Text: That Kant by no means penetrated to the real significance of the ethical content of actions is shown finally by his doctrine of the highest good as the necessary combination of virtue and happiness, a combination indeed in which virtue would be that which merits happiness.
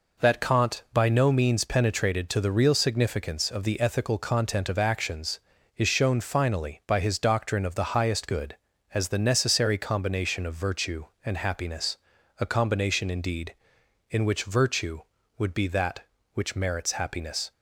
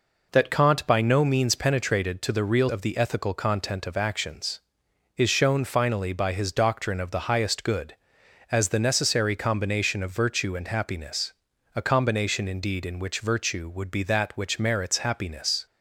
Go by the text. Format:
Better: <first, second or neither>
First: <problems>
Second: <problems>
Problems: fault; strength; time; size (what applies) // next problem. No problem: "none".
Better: first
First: none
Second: skips "significance"; at 2.6 s